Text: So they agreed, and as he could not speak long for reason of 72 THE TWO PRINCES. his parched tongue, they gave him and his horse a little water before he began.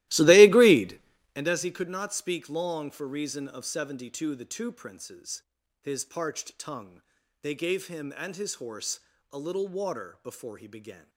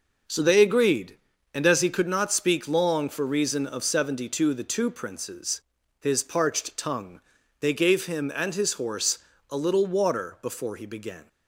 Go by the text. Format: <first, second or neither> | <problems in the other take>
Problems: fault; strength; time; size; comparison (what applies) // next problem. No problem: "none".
second | starts louder than the rest; strong; until 1.5 s; 17 dB // pauses between "horse" and "a"; slight; at 9.0 s; 0.28 s long; slight in the second